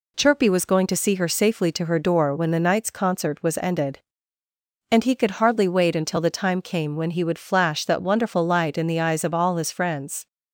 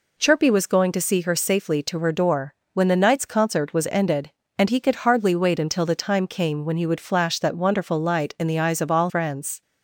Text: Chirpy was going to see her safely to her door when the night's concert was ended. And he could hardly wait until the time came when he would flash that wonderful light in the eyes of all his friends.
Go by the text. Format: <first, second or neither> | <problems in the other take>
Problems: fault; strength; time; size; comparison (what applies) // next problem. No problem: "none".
first | pauses between "door" and "when"; slight; at 2.5 s; 0.18 s long // skips "his"; at 9.0 s